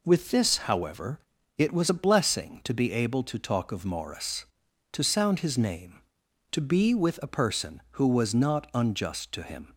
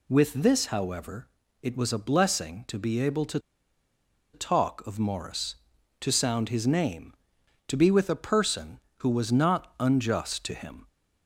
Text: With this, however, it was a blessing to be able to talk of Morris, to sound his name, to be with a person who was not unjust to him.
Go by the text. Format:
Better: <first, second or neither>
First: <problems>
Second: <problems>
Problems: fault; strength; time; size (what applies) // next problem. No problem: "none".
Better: first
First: none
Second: pauses between "to" and "talk"; noticeable; at 3.3 s; 0.94 s long